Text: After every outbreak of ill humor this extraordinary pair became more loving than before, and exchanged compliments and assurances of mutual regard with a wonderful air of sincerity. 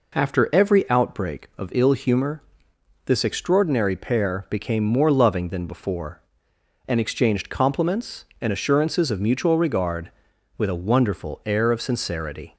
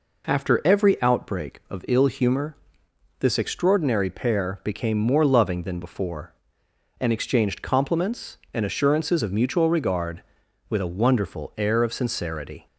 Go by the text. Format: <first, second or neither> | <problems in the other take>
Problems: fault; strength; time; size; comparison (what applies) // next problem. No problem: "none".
neither | pauses between "humor" and "this"; noticeable; the same in both